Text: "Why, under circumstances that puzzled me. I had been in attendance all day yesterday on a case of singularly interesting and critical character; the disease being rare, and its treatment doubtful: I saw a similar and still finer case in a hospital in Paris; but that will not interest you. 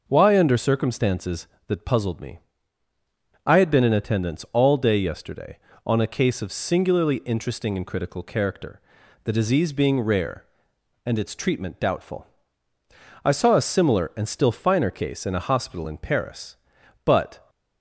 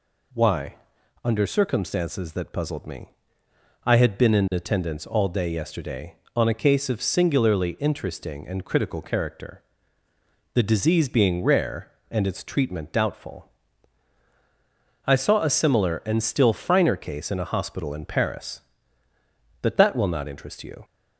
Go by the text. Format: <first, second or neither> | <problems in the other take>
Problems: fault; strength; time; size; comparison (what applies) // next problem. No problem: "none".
second | stops before "that will not interest you"; at 17.4 s